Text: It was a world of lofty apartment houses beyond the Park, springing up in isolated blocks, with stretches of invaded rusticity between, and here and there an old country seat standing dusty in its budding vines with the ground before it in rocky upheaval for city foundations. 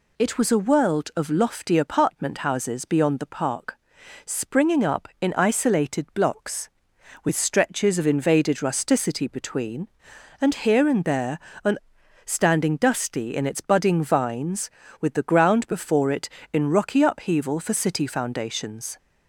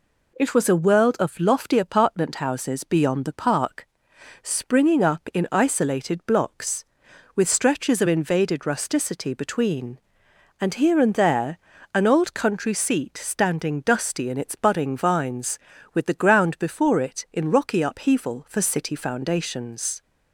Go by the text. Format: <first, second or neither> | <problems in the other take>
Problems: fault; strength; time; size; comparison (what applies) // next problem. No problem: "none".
second | pauses between "there" and "an"; slight; at 11.3 s; 0.28 s long; slight in the second // skips "old country seat"; at 12.0 s